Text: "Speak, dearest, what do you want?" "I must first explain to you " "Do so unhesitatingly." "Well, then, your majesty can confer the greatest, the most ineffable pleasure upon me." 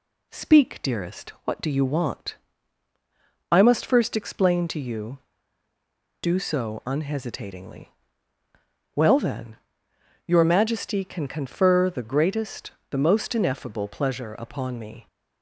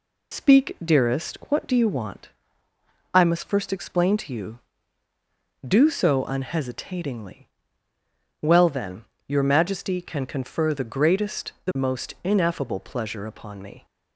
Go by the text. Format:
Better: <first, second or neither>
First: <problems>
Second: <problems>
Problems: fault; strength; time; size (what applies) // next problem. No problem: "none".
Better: first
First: none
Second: loses the start of "Speak"; at 0.3 s; 60 ms